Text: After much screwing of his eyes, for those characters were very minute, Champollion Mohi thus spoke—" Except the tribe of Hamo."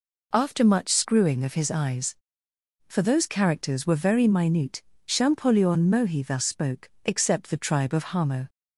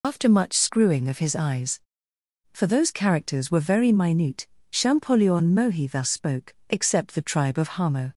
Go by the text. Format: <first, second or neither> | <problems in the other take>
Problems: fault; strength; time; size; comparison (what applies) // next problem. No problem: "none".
first | loses the start of "After"; at 0.0 s; 75 ms